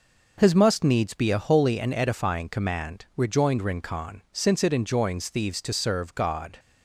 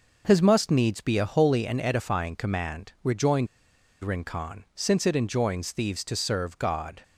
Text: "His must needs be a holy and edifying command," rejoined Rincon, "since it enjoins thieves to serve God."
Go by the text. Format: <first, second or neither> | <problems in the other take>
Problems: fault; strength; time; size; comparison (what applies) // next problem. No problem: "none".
first | pauses between "rejoined" and "Rincon"; noticeable; at 3.4 s; 0.55 s long